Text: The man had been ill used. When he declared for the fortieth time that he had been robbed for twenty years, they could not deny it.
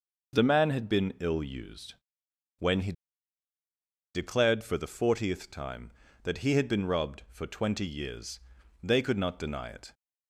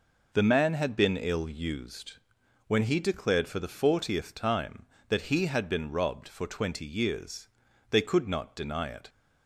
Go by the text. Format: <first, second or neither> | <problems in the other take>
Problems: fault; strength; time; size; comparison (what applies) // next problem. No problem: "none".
second | pauses between "he" and "declared"; at 2.9 s; 1.2 s long